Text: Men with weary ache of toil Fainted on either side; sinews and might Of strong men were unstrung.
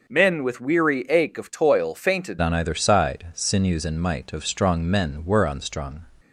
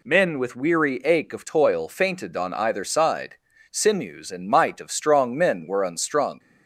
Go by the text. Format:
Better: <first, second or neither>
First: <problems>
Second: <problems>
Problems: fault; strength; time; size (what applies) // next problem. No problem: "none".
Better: second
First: starts louder than the rest; noticeable; until 1.1 s; 6 dB // changes voice at "on"; from 2.4 s on; 3.6 s long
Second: none